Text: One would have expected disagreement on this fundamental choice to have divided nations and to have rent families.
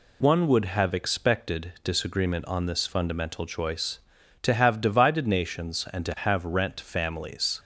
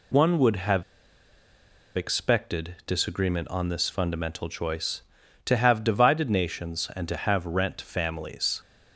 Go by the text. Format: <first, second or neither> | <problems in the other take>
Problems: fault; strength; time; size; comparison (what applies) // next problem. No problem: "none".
first | pauses between "have" and "expected"; at 0.8 s; 1.1 s long